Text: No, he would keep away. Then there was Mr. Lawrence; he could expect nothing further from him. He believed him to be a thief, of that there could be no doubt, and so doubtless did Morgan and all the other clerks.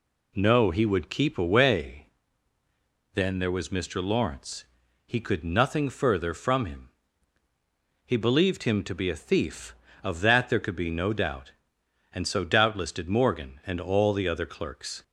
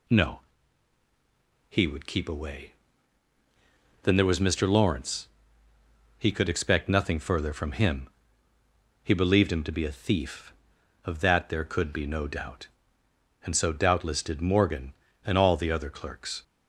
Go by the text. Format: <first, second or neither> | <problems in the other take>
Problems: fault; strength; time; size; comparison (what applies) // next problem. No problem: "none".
second | skips "expect"; at 5.4 s